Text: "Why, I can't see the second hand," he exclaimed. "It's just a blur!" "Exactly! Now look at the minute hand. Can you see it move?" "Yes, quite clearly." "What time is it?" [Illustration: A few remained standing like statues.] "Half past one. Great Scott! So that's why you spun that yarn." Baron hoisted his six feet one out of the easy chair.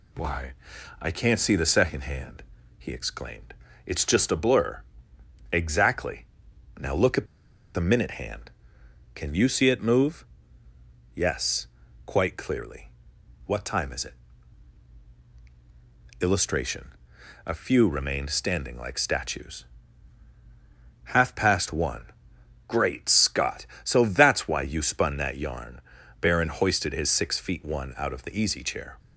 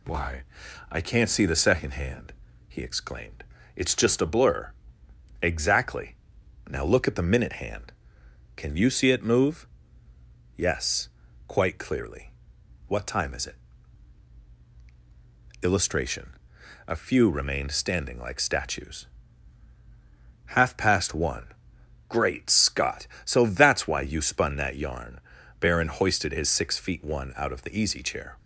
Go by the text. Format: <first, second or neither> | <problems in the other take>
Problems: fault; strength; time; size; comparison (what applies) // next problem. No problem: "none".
second | pauses between "at" and "the"; noticeable; at 7.2 s; 0.48 s long